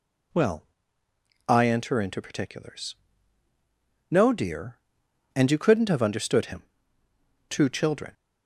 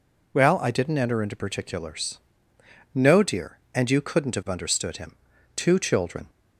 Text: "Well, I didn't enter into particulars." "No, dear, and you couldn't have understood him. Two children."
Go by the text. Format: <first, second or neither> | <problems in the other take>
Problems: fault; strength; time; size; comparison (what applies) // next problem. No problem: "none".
second | skips "didn't"; at 1.6 s